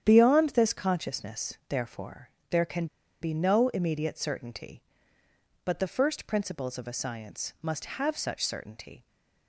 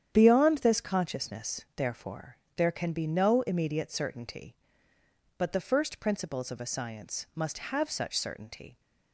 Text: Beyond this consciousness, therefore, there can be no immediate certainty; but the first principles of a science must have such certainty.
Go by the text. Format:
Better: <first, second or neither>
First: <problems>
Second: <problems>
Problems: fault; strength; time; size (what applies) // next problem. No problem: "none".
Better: second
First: starts louder than the rest; strong; until 1.0 s; 9 dB // pauses between "can" and "be"; slight; at 2.8 s; 0.35 s long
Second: starts louder than the rest; strong; until 1.1 s; 9 dB